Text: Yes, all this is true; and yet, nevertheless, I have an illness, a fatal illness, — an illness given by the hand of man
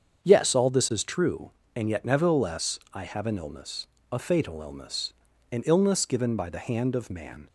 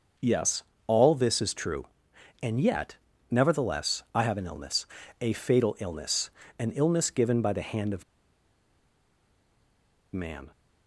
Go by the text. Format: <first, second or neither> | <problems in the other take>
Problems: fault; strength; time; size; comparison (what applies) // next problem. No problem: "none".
first | starts louder than the rest; until 1.4 s; 6 dB; strong in the first // pauses between "of" and "man"; strong; at 8.0 s; 2.0 s long